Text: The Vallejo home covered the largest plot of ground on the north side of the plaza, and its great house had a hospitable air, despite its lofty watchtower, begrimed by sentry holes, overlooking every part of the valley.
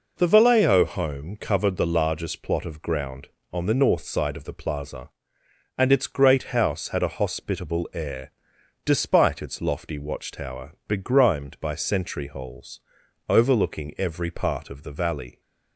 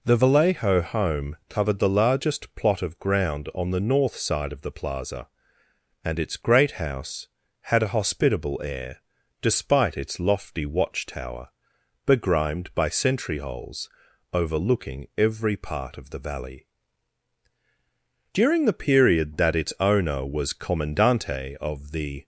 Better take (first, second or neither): first